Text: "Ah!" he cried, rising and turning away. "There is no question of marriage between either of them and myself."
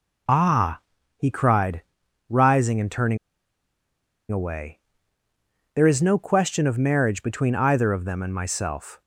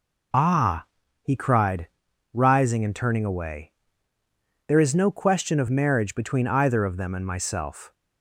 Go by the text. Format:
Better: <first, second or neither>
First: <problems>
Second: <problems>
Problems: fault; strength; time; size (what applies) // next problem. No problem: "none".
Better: second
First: pauses between "turning" and "away"; at 3.1 s; 1.1 s long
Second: none